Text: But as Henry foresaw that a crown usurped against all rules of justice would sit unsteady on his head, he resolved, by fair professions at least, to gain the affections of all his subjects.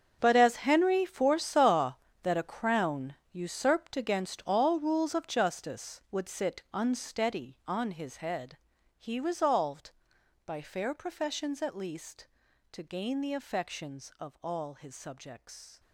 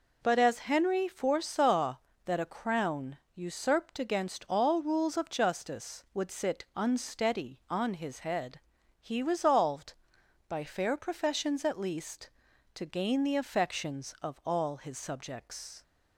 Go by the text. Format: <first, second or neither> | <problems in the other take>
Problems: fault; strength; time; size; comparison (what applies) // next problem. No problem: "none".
second | gets quieter; strong; throughout; 15.5 dB // pauses between "crown" and "usurped"; slight; at 3.1 s; 0.16 s long; slight in the second